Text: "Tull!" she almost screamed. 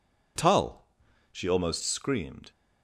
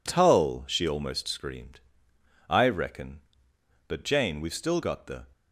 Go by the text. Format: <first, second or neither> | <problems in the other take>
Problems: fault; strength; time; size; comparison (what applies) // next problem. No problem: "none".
first | goes on to say "I reckon But Jane we've still got the"; strong; from 2.4 s on; 2.7 s long